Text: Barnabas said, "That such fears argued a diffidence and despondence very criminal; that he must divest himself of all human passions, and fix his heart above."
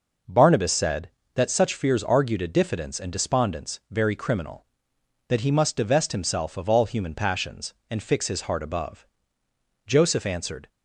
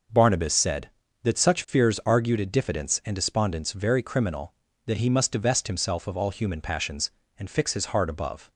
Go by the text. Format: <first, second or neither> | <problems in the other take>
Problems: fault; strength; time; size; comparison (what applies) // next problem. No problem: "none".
second | goes on to say "Joseph answered"; noticeable; from 9.8 s on; 0.82 s long